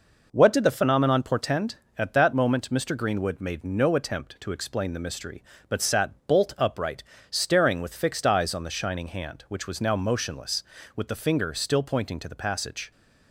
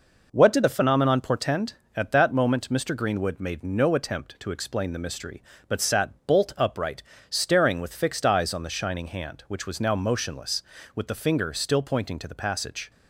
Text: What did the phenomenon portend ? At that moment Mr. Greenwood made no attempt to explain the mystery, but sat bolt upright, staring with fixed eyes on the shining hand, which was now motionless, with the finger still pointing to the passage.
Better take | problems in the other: neither | none

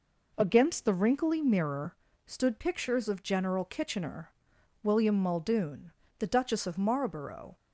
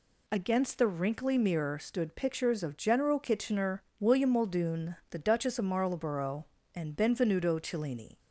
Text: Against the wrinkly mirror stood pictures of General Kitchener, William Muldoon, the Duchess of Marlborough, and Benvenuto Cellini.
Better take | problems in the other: second | pauses between "mirror" and "stood"; slight; at 1.9 s; 0.30 s long // stops before "and Benvenuto Cellini"; at 7.5 s

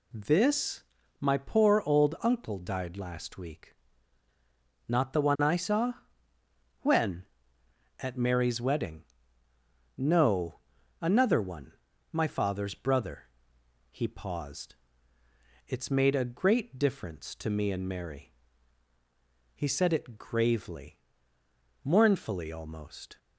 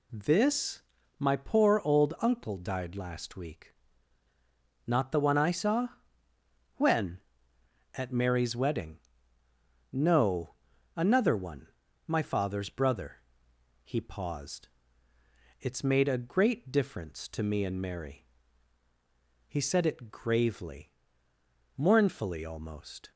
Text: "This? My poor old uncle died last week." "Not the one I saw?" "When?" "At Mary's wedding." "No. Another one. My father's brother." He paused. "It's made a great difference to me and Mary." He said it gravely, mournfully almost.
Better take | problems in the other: neither | none

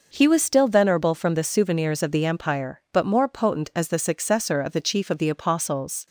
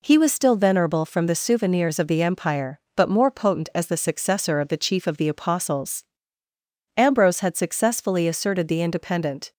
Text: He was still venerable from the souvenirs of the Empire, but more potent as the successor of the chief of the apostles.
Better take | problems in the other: first | goes on to say "Ambrose had successfully asserted the independent"; strong; from 6.9 s on; 2.5 s long

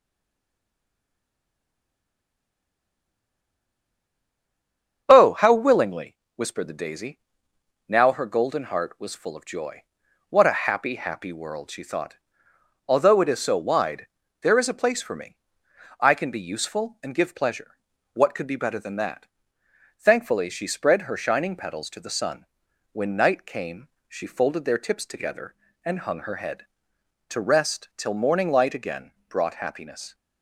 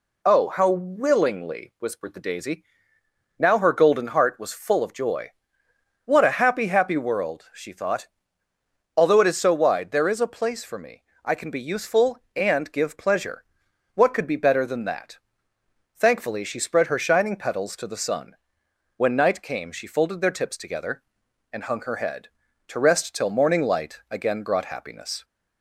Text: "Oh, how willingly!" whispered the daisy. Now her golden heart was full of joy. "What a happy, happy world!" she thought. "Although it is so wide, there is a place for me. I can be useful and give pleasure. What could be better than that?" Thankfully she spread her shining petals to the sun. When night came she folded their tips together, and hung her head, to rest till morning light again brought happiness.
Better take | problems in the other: second | stays silent before the first word; strong; until 5.0 s; 5.0 s long // starts louder than the rest; strong; until 6.0 s; 7 dB // pauses between "came" and "she"; slight; at 23.8 s; 0.18 s long // pauses between "again" and "brought"; slight; at 29.1 s; 0.18 s long

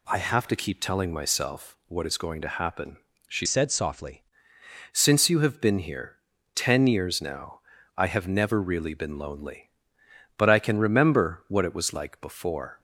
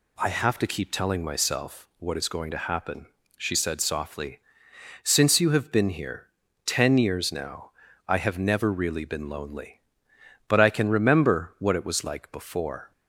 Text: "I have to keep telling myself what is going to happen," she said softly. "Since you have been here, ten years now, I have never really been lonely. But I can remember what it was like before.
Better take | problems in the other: second | changes voice from "said" to "softly"; from 3.4 to 4.2 s; 0.8 s long

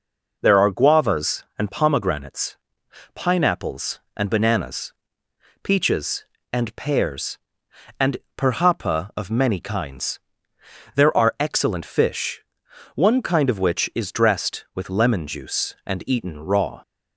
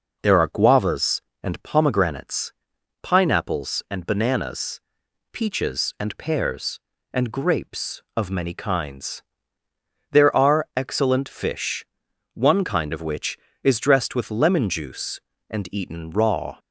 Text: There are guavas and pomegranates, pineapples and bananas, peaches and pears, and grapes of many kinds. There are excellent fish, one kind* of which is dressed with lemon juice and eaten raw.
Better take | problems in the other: second | says "perhapa" for "grapes"; at 8.3 s

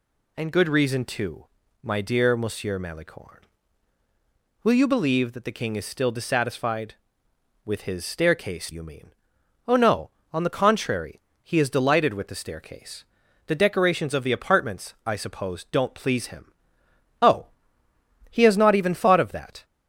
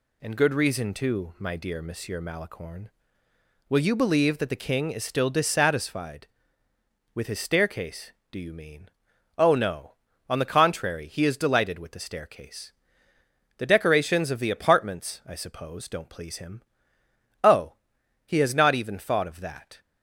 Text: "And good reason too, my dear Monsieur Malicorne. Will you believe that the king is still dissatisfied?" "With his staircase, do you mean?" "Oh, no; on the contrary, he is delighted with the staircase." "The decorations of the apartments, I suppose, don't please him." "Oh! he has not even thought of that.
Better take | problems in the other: second | skips "do"; at 8.7 s

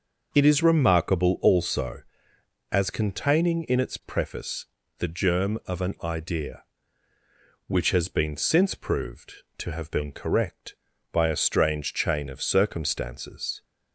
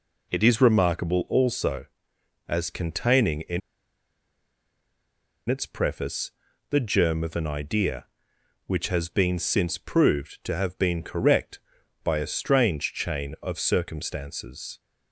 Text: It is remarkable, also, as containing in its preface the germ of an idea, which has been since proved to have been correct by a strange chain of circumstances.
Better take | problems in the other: first | pauses between "in" and "its"; strong; at 3.6 s; 1.8 s long // pauses between "preface" and "the"; at 6.3 s; 0.38 s long; slight in the first

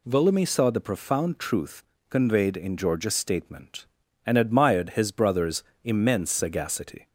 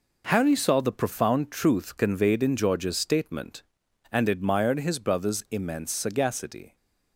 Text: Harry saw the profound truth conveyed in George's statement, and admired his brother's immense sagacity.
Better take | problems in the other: second | says "Volumi" for "Harry"; at 0.0 s // pauses between "truth" and "conveyed"; slight; at 1.8 s; 0.26 s long // pauses between "brother's" and "immense"; slight; at 5.6 s; 0.22 s long

